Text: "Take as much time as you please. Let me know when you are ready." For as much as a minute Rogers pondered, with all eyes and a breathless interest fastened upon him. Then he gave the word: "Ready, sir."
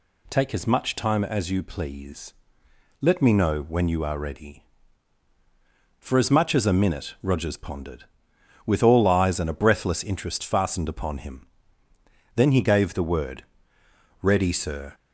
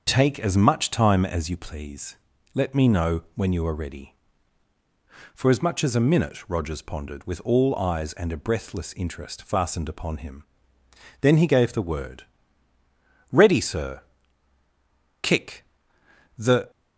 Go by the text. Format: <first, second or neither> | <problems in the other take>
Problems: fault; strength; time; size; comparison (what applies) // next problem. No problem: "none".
first | starts louder than the rest; until 1.0 s; 6.5 dB // goes on to say "Kick The"; from 15.2 s on; 1.5 s long